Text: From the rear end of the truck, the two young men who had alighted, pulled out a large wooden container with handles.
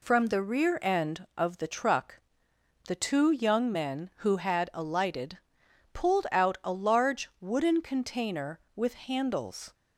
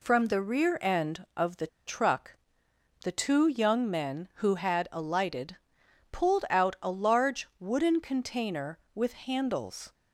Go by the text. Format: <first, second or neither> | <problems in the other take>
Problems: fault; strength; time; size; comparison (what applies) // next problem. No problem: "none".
first | pauses between "the" and "truck"; slight; at 1.6 s; 0.19 s long